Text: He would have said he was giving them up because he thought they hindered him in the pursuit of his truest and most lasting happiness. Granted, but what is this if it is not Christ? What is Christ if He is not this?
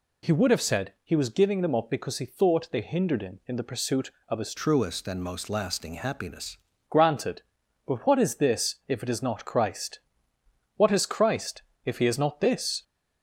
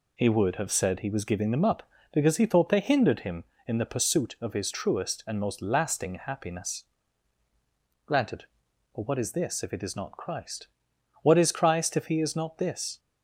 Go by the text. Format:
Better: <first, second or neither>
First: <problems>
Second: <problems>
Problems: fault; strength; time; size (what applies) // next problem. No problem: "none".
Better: second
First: changes voice from "truest" to "happiness"; from 4.5 to 6.5 s; 2.0 s long // pauses between "Christ" and "if"; slight; at 11.6 s; 0.24 s long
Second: none